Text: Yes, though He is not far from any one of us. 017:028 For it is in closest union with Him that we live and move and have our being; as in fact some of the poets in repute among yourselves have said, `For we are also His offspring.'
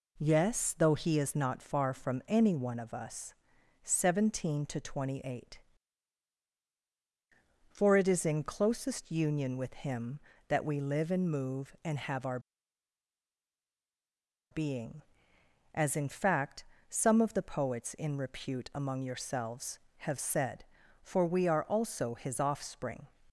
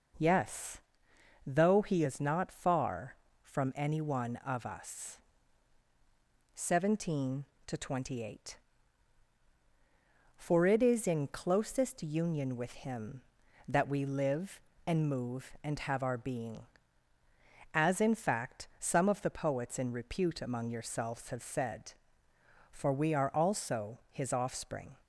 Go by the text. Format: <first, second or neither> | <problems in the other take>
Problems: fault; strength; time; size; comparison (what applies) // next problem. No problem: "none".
second | pauses between "our" and "being"; strong; at 12.3 s; 2.1 s long // pauses between "fact" and "some"; slight; at 16.6 s; 0.26 s long